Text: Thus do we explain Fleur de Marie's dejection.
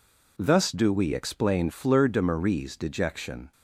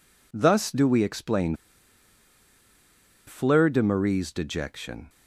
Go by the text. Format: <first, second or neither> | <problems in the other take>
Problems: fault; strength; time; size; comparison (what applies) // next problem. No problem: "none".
first | pauses between "explain" and "Fleur"; strong; at 1.5 s; 1.7 s long